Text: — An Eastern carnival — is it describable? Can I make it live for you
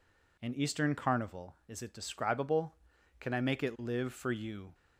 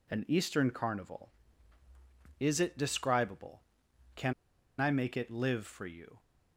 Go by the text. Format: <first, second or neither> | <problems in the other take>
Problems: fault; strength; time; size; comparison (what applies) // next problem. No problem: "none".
first | pauses between "Can" and "I"; noticeable; at 4.3 s; 0.46 s long